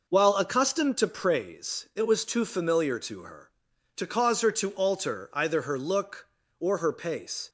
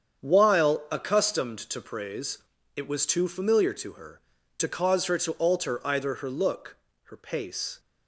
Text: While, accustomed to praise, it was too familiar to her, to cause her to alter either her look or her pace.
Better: first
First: none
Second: starts louder than the rest; strong; until 1.3 s; 8 dB // skips "or"; at 6.8 s

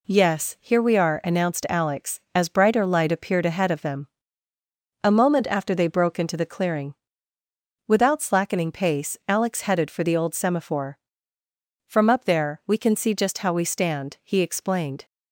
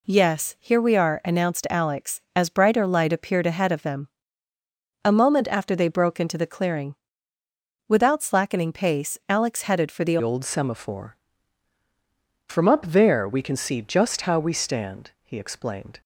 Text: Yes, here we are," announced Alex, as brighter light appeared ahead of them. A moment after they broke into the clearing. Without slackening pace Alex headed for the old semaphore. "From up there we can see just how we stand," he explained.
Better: first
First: none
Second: changes voice at "old"; from 10.2 s on; 5.8 s long

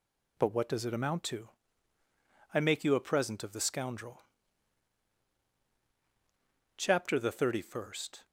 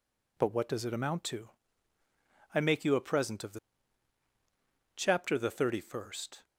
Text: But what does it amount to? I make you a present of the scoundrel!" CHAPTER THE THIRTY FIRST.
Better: first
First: none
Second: skips "scoundrel"; at 4.2 s

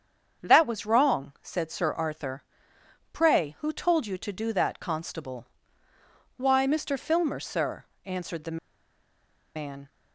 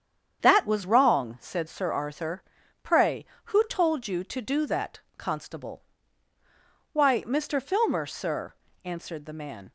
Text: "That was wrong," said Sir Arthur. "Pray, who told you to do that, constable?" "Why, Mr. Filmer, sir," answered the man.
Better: second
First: starts louder than the rest; strong; until 1.5 s; 7.5 dB // pauses between "the" and "man"; noticeable; at 8.5 s; 0.98 s long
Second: starts louder than the rest; strong; until 1.5 s; 8 dB

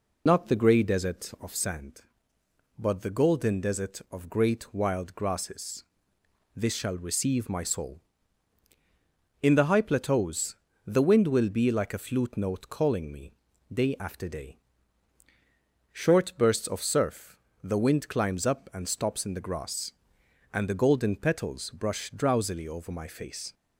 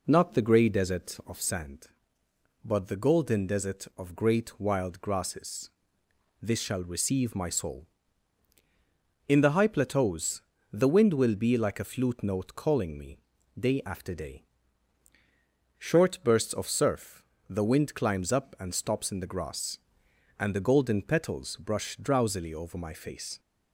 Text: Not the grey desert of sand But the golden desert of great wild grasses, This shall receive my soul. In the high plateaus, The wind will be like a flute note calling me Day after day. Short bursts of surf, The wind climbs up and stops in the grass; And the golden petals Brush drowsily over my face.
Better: second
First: loses the start of "Not"; at 0.2 s; 50 ms // pauses between "me" and "Day"; at 13.3 s; 0.42 s long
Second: pauses between "me" and "Day"; at 13.1 s; 0.42 s long

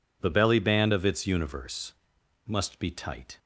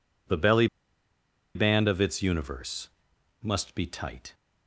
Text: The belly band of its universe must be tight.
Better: first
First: pauses between "universe" and "must"; noticeable; at 1.9 s; 0.54 s long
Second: pauses between "belly" and "band"; noticeable; at 0.6 s; 0.87 s long // pauses between "universe" and "must"; noticeable; at 2.8 s; 0.54 s long

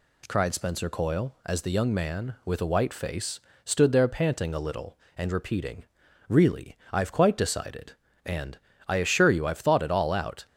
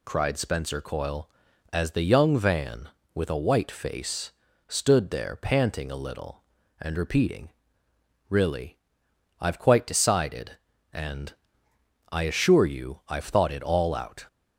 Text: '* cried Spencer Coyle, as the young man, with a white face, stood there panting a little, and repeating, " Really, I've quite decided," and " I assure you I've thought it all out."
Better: first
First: none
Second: says "van" for "man"; at 2.3 s

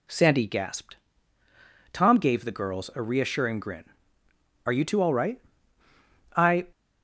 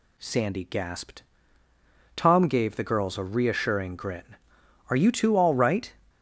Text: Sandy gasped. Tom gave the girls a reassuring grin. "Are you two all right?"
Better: second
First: goes on to say "I"; slight; from 6.3 s on; 0.34 s long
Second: none

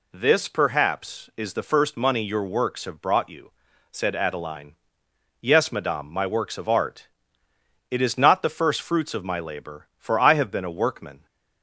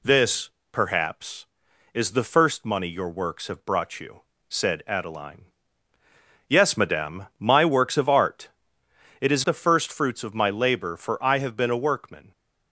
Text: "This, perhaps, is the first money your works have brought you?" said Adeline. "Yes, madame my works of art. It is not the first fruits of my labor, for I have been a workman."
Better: first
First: none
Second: skips "not"; at 9.4 s

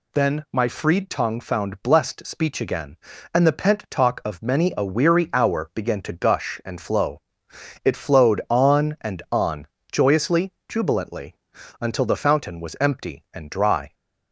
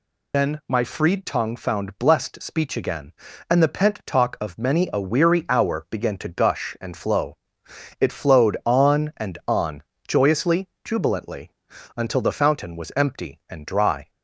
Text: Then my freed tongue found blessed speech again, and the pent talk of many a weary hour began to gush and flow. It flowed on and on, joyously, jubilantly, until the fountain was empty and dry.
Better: first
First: none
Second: loses the start of "Then"; at 0.3 s; 50 ms

